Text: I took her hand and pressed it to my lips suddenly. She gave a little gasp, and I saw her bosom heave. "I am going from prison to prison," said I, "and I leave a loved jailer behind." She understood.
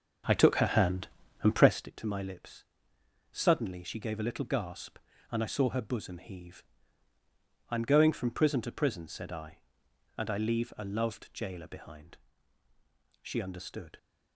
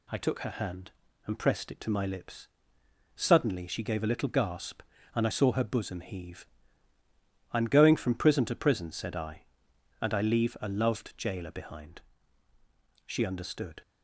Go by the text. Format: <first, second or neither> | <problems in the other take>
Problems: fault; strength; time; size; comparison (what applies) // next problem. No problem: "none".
second | starts louder than the rest; until 1.9 s; 6.5 dB // pauses between "lips" and "suddenly"; noticeable; at 2.6 s; 0.66 s long; noticeable in the second